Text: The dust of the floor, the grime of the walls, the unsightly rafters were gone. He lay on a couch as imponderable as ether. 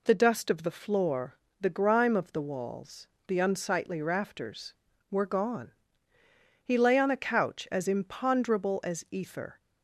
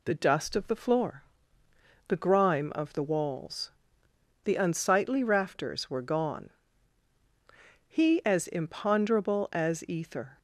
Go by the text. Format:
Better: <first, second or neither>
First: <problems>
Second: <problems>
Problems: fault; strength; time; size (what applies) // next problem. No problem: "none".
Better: first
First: none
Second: skips "lay on a couch"; at 8.2 s